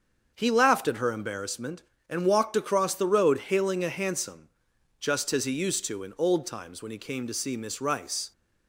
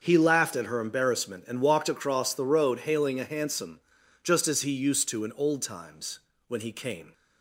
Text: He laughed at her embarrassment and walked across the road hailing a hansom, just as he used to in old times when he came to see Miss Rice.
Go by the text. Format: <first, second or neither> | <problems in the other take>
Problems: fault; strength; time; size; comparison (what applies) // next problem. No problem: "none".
first | starts louder than the rest; until 1.0 s; 6.5 dB; also in the first // pauses between "times" and "when"; slight; at 6.2 s; 0.26 s long // stops before "to see Miss Rice"; at 7.1 s